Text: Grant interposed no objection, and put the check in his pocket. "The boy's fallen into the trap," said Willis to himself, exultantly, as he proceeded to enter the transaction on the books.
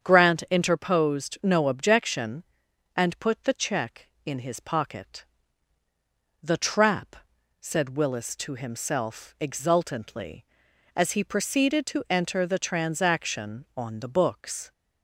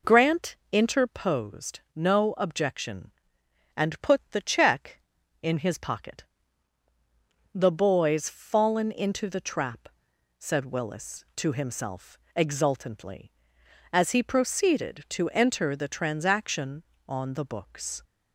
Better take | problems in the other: second | starts louder than the rest; strong; until 1.0 s; 8 dB // skips "The boy's fallen into"; at 5.8 s

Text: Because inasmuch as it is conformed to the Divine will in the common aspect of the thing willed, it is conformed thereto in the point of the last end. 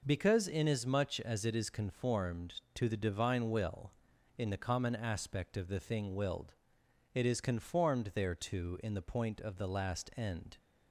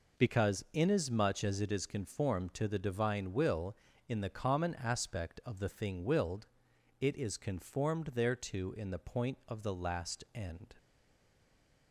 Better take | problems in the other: first | stays silent after the last word; from 10.7 s on; 1.2 s long

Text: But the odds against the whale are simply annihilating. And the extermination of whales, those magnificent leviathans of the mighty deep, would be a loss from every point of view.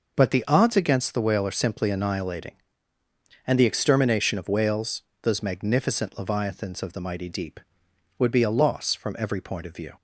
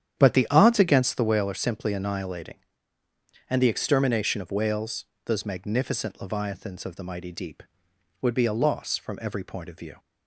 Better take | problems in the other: first | starts louder than the rest; strong; until 1.5 s; 9.5 dB

